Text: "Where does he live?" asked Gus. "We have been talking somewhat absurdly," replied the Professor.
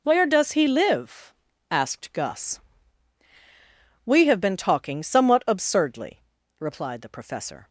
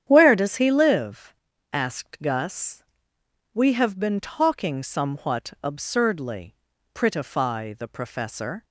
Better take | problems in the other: first | starts louder than the rest; strong; until 1.0 s; 9.5 dB // says "prettify" for "replied"; at 6.9 s

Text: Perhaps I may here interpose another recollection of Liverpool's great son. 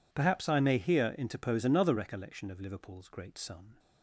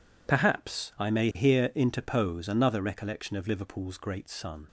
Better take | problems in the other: neither | none

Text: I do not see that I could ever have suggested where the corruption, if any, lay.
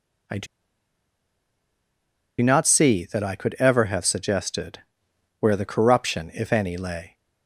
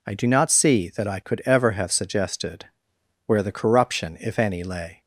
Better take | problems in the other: second | pauses between "do" and "not"; strong; at 0.4 s; 1.9 s long // pauses between "suggested" and "where"; noticeable; at 4.7 s; 0.60 s long; noticeable in the second

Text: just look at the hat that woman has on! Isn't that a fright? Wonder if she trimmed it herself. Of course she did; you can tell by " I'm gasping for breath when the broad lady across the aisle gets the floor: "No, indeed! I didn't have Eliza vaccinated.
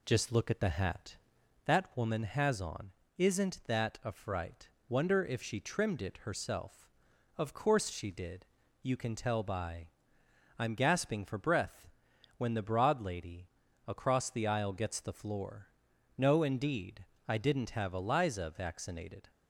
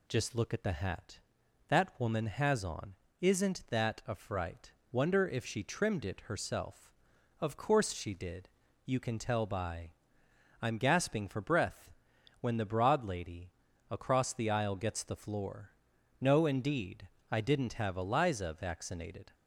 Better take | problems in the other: second | starts louder than the rest; slight; until 1.7 s; 2 dB // pauses between "breath" and "when"; noticeable; at 11.8 s; 0.48 s long; noticeable in the second // pauses between "lady" and "across"; at 13.4 s; 0.40 s long; also in the second

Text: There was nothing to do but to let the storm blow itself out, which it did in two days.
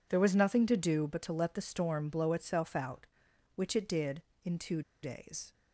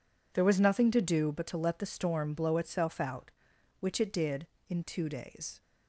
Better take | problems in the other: second | pauses between "two" and "days"; slight; at 4.8 s; 0.21 s long

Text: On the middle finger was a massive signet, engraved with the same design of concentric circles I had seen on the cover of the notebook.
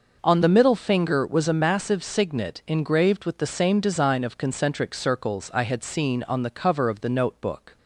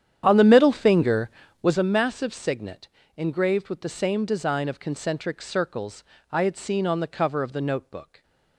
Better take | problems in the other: first | starts louder than the rest; strong; until 1.8 s; 9.5 dB // pauses between "circles" and "I"; slight; at 6.0 s; 0.30 s long

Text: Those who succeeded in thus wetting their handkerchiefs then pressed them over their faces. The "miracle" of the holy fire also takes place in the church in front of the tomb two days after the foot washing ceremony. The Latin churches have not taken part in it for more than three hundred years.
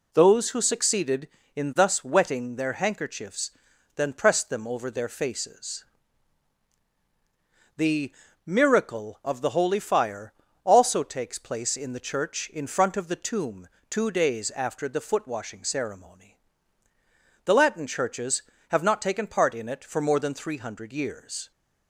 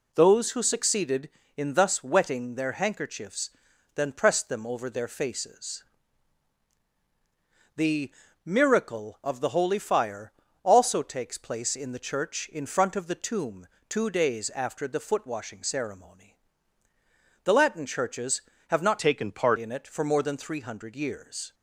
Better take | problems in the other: first | pauses between "handkerchiefs" and "then"; at 3.4 s; 0.44 s long; also in the first // pauses between "The" and "miracle"; slight; at 8.1 s; 0.32 s long; slight in the first // pauses between "fire" and "also"; slight; at 10.3 s; 0.30 s long; slight in the first // pauses between "tomb" and "two"; slight; at 13.6 s; 0.22 s long; slight in the first // changes voice from "taken" to "part"; from 18.9 to 19.5 s; 0.6 s long

